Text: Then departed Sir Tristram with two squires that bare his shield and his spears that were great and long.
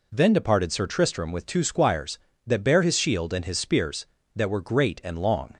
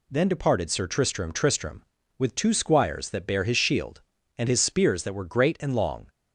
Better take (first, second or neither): first